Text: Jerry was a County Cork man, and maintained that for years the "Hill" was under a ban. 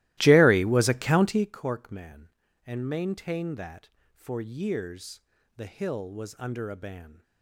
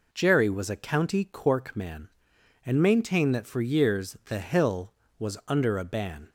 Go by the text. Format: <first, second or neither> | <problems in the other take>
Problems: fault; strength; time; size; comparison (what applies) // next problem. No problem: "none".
second | starts louder than the rest; strong; until 1.6 s; 17 dB // pauses between "years" and "the"; slight; at 5.2 s; 0.34 s long